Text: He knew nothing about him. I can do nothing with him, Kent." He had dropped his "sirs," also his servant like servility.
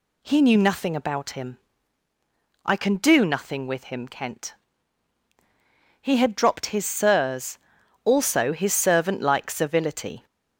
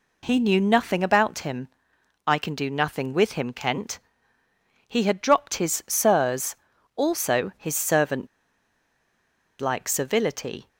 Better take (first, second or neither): first